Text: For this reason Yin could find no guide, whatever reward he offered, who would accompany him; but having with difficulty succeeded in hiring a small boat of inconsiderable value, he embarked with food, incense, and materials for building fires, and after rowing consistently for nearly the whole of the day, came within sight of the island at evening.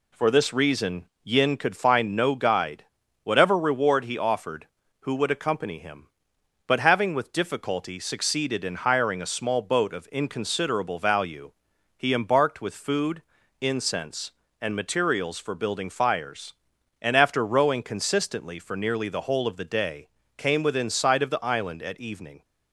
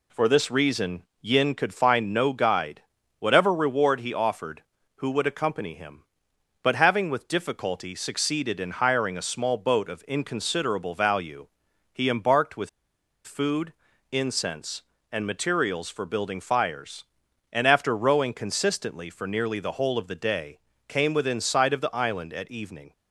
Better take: first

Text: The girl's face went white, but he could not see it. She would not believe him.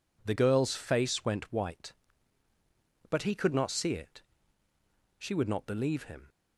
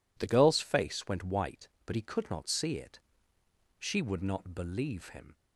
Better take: neither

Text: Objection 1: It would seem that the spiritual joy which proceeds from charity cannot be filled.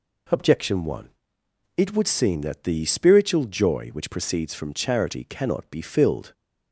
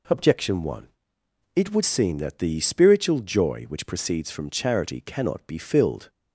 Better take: neither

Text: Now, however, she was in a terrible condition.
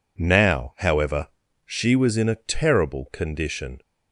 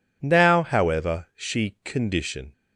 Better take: first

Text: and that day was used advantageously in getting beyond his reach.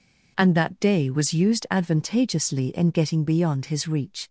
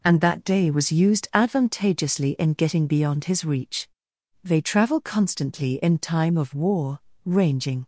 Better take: first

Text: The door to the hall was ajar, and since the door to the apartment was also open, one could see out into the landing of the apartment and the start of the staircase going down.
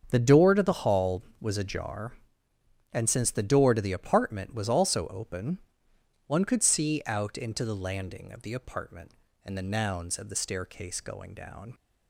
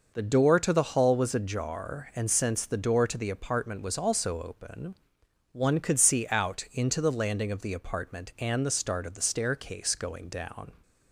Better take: second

